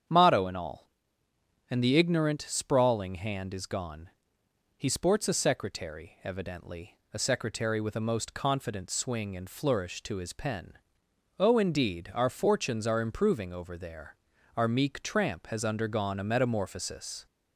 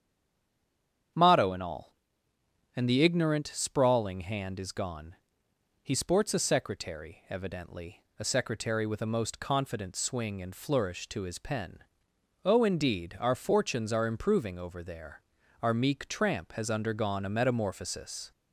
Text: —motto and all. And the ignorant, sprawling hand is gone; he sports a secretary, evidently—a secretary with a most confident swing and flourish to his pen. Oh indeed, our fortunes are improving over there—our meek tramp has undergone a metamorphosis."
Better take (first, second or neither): first